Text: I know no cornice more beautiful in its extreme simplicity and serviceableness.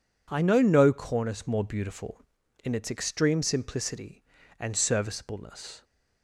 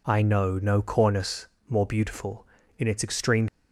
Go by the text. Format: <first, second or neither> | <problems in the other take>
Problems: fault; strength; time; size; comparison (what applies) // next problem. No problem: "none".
first | pauses between "cornice" and "more"; slight; at 1.4 s; 0.20 s long // stops before "simplicity and serviceableness"; at 3.4 s